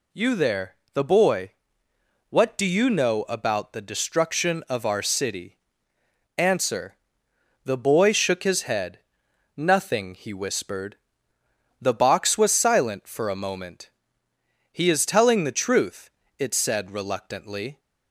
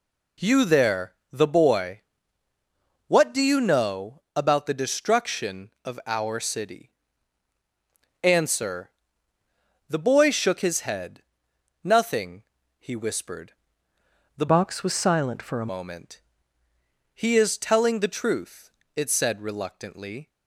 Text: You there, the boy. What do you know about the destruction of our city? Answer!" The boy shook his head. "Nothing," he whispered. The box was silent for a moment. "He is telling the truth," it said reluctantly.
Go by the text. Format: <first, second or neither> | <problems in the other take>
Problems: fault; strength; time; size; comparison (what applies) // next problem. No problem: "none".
first | pauses between "know" and "about"; slight; at 4.2 s; 0.16 s long // changes voice from "box" to "a"; from 14.4 to 15.6 s; 1.2 s long